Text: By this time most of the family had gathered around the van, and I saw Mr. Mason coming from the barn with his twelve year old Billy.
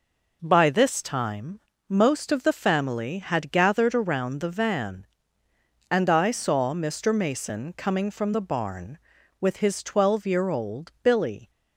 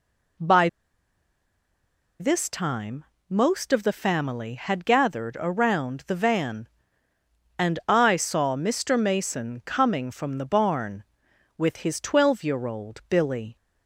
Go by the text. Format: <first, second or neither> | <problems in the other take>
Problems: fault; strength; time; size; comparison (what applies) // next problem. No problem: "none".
first | pauses between "By" and "this"; strong; at 0.6 s; 1.5 s long // pauses between "time" and "most"; slight; at 3.0 s; 0.26 s long; slight in the first